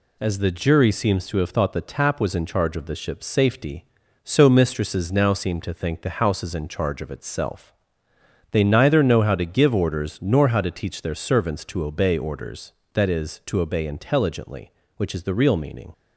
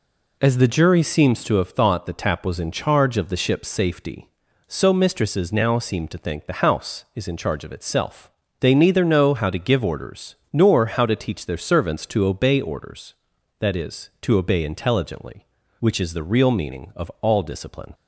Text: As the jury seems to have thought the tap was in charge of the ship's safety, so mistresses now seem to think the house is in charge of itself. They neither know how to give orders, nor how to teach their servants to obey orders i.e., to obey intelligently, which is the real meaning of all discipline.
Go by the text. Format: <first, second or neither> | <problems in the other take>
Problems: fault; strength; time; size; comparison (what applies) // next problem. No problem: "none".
second | stops before "of all discipline"; at 15.9 s